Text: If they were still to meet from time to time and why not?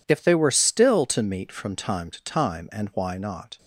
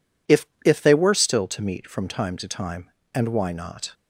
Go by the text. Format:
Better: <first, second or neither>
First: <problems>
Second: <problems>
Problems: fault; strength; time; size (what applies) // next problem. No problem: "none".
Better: first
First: none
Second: says "If" twice; at 0.6 s